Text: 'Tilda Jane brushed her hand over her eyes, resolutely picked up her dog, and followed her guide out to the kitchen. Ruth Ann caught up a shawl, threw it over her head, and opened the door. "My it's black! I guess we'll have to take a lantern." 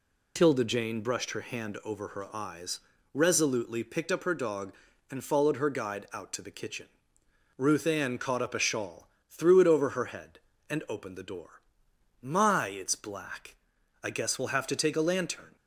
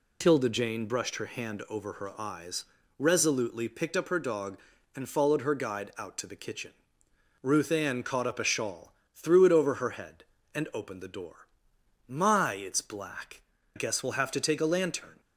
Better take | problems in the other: first | skips "I"; at 13.5 s

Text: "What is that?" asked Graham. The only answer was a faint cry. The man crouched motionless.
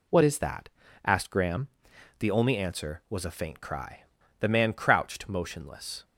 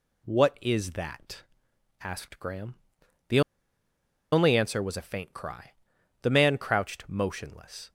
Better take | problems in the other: first | pauses between "The" and "only"; noticeable; at 3.4 s; 0.91 s long

